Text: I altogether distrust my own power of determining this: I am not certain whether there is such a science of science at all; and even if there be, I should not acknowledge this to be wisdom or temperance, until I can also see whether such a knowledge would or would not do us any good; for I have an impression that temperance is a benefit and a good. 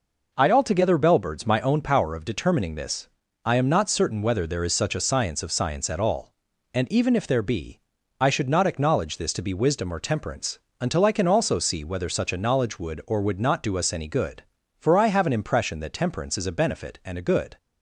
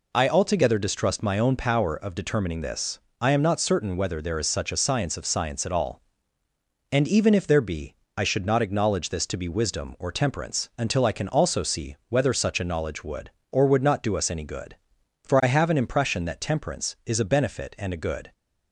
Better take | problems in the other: second | says "bellbirds" for "distrust"; at 0.9 s

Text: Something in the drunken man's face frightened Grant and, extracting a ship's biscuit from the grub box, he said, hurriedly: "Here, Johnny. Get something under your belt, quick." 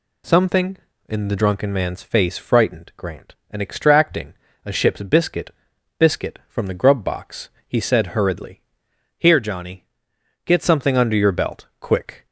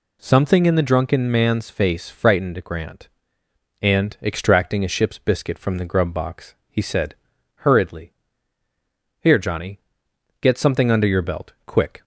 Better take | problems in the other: second | pauses between "extracting" and "a"; slight; at 4.3 s; 0.32 s long // says "biscuit" twice; at 5.9 s

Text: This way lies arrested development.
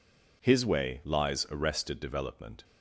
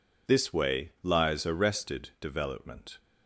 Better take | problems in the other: second | says "His" for "This"; at 0.4 s

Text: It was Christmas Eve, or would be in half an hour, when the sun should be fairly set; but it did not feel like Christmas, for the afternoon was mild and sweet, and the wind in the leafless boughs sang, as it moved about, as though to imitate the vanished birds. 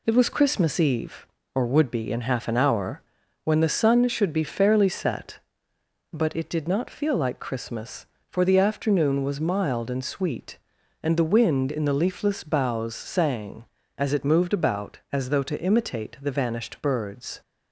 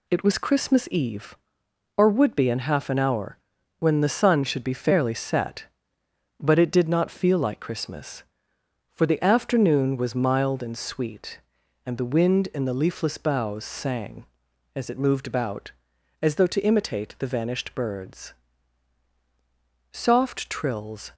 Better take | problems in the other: first | goes on to say "Soft trills"; noticeable; from 19.9 s on; 1.2 s long

